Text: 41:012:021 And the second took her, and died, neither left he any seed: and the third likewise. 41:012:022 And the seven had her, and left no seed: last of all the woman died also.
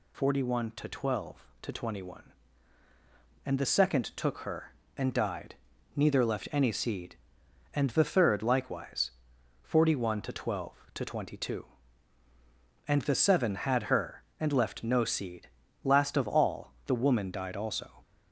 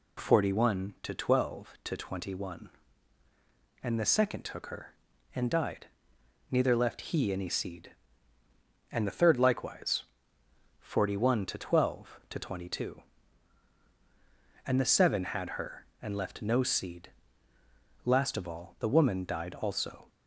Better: second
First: skips "he"; at 6.5 s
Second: none

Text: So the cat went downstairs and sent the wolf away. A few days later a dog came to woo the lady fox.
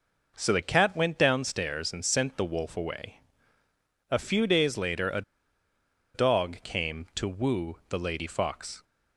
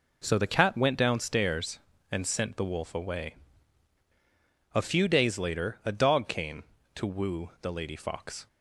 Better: second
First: pauses between "a" and "dog"; noticeable; at 5.2 s; 0.93 s long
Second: none

